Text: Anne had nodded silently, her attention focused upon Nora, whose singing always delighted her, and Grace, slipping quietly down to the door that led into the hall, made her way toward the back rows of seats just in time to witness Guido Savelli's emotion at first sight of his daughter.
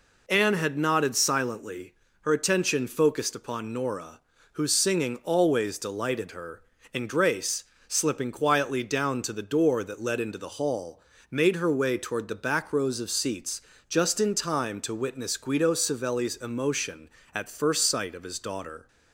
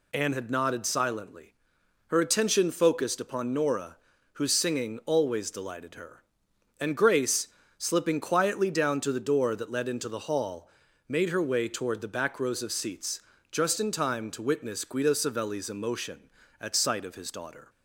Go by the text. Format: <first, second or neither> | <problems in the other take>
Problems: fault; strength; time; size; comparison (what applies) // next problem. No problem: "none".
first | pauses between "seats" and "just"; slight; at 13.1 s; 0.32 s long; slight in the first // skips "first"; at 16.7 s